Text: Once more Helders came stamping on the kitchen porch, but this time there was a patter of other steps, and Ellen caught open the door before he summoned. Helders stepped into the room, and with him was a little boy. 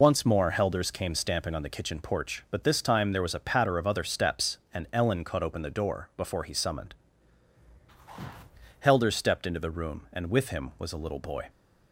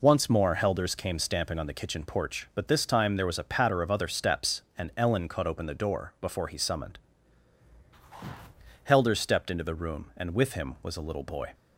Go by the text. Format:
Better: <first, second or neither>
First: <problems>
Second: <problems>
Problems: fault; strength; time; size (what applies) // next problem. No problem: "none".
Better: second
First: loses the start of "Once"; at 0.0 s; 25 ms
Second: none